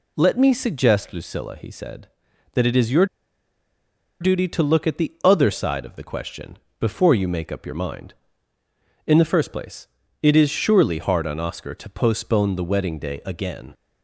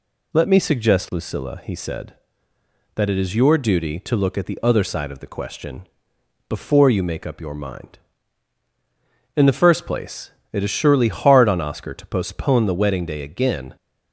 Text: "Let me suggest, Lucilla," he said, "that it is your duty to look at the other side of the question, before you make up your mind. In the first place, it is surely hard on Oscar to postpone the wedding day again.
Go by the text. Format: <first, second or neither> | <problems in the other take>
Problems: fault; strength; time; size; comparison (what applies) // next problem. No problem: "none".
second | pauses between "your" and "duty"; at 3.0 s; 1.1 s long